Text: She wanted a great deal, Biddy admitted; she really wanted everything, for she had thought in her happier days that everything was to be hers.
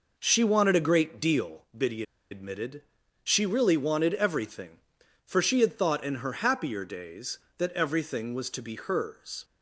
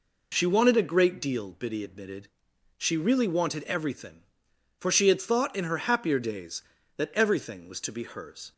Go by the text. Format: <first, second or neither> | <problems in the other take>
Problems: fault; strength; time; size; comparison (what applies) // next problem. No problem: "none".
second | pauses between "Biddy" and "admitted"; slight; at 2.0 s; 0.28 s long